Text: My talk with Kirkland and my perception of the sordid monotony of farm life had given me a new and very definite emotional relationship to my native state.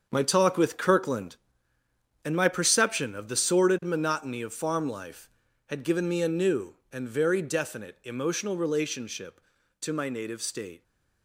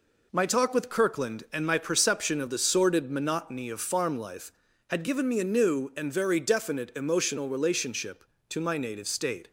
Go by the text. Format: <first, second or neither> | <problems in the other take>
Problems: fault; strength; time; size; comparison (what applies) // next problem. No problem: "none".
second | gets quieter; strong; throughout; 9.5 dB